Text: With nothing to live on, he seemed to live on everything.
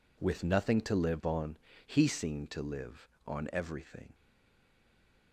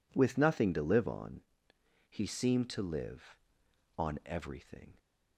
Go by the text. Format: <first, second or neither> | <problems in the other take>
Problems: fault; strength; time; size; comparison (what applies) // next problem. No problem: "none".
second | stays silent after the last word; noticeable; from 4.1 s on; 1.2 s long